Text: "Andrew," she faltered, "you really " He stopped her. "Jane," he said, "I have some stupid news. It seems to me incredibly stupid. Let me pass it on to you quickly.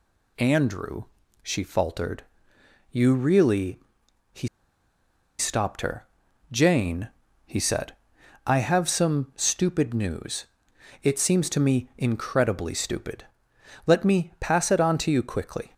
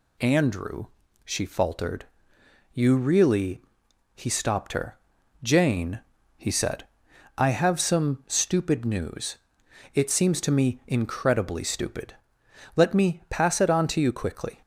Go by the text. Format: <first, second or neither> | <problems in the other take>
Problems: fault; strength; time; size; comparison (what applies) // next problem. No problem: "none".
second | pauses between "He" and "stopped"; noticeable; at 4.4 s; 0.91 s long